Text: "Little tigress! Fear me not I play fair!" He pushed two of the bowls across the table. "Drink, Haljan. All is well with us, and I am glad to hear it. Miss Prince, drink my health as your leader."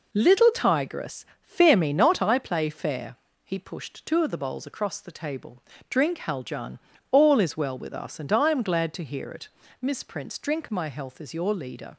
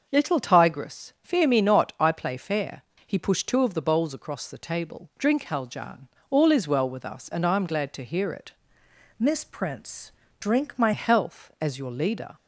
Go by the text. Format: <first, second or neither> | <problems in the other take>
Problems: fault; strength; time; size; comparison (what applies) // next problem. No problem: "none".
first | starts louder than the rest; until 1.1 s; 6.5 dB // changes voice from "Miss" to "my"; from 9.1 to 10.9 s; 1.8 s long